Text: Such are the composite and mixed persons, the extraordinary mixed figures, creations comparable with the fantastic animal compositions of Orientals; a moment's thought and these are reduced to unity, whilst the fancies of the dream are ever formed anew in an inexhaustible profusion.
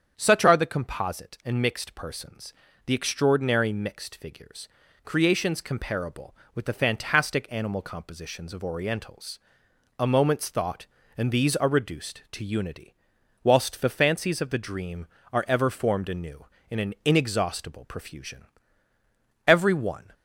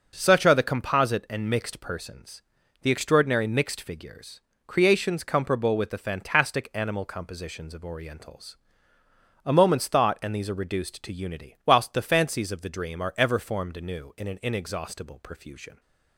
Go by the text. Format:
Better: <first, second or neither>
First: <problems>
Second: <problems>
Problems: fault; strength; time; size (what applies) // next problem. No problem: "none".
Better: second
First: starts louder than the rest; strong; until 1.1 s; 7.5 dB // goes on to say "Every one"; noticeable; from 19.4 s on; 0.66 s long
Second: starts louder than the rest; noticeable; until 1.1 s; 6 dB